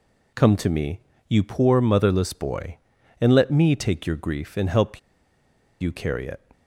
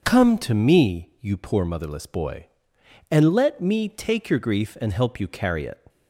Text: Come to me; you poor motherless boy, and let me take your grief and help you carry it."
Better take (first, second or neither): second